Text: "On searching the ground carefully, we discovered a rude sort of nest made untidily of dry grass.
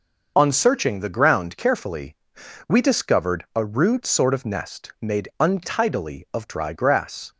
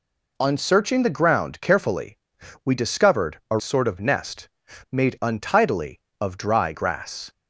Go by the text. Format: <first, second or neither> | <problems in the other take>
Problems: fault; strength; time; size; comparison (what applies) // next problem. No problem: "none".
first | skips "rude"; at 3.5 s // pauses between "nest" and "made"; at 4.4 s; 0.44 s long